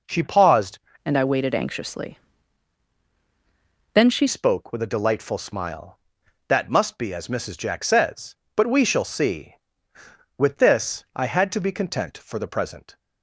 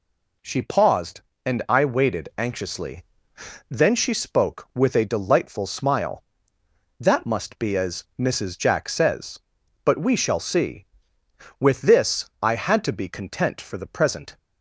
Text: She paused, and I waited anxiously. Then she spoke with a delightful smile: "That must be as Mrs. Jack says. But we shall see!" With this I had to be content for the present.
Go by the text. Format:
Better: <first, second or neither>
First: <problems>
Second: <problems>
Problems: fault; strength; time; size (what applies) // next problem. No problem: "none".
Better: second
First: changes voice from "and" to "she"; from 1.0 to 4.2 s; 3.2 s long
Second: none